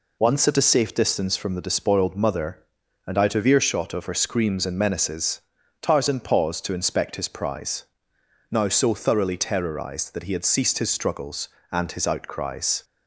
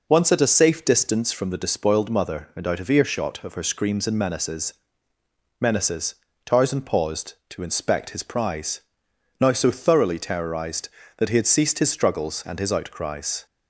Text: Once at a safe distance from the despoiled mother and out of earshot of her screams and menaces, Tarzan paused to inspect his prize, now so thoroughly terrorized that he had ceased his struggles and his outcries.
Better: first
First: none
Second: says "menaces" twice; at 5.6 s

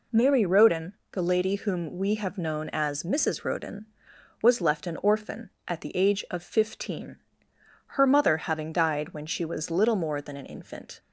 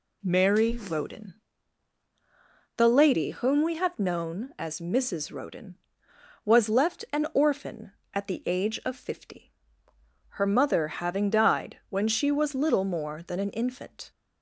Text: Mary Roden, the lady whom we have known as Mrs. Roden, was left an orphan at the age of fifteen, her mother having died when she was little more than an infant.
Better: first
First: none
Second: says "fifty" for "fifteen"; at 8.9 s

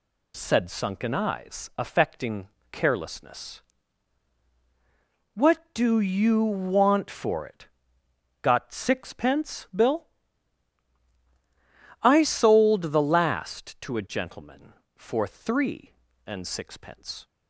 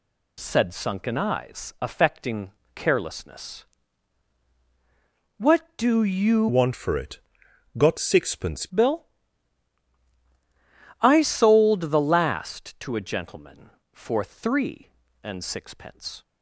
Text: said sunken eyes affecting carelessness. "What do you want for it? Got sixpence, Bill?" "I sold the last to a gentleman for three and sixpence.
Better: first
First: pauses between "affecting" and "carelessness"; slight; at 2.4 s; 0.24 s long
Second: pauses between "affecting" and "carelessness"; slight; at 2.5 s; 0.24 s long // changes voice from "want" to "sixpence"; from 6.4 to 8.6 s; 2.2 s long

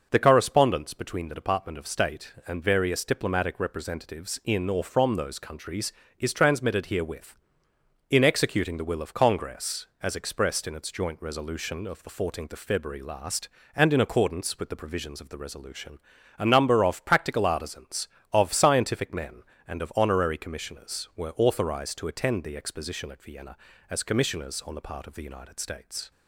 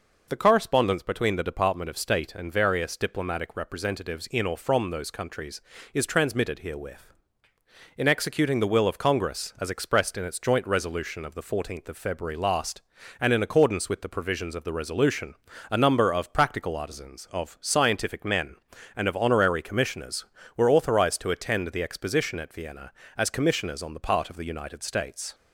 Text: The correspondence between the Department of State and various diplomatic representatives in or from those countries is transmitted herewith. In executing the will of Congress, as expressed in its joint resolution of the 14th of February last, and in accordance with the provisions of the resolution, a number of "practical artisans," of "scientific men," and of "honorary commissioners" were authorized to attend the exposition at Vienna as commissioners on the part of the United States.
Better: neither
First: none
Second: none

